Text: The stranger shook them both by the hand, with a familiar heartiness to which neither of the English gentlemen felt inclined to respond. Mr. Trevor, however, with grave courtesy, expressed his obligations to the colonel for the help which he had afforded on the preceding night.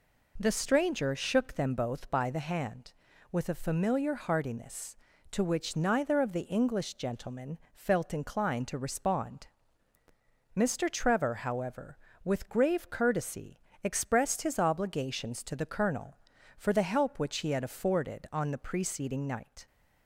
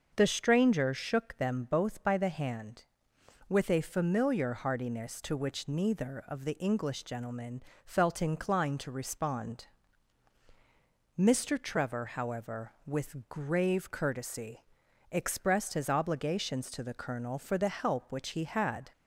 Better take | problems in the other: first | starts louder than the rest; until 1.1 s; 6.5 dB // pauses between "gentlemen" and "felt"; slight; at 7.6 s; 0.20 s long; slight in the first // stops before "afforded on the preceding night"; at 18.9 s

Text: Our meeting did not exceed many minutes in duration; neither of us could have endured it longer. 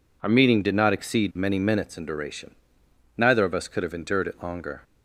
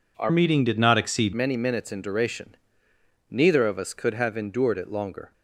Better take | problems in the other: first | changes voice from "meeting" to "exceed"; from 0.2 to 1.3 s; 1.1 s long

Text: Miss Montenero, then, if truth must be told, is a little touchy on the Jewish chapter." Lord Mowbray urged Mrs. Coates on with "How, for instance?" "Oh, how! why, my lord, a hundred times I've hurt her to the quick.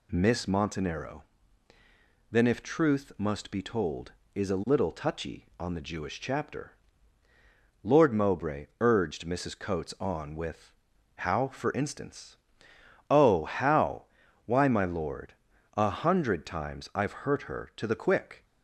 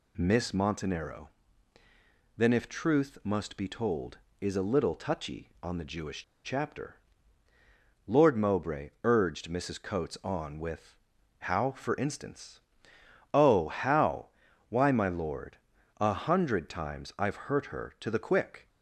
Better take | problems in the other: first | pauses between "Jewish" and "chapter"; slight; at 6.2 s; 0.20 s long // pauses between "with" and "How"; at 10.9 s; 0.44 s long; also in the first

